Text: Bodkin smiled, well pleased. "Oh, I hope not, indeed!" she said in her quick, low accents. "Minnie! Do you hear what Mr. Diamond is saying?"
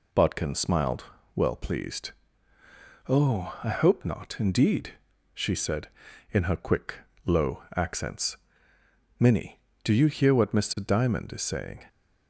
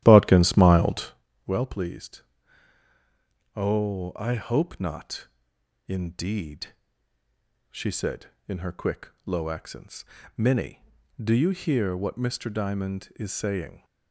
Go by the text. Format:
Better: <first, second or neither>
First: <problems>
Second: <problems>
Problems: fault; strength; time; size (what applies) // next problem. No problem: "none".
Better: first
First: none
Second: starts louder than the rest; strong; until 1.2 s; 13 dB